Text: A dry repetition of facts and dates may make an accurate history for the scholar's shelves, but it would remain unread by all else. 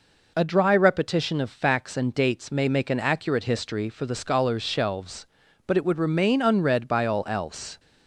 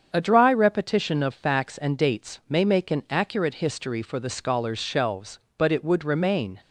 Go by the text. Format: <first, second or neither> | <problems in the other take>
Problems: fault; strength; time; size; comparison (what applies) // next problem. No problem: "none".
first | starts louder than the rest; strong; until 1.1 s; 7.5 dB // stops before "unread by all else"; at 6.6 s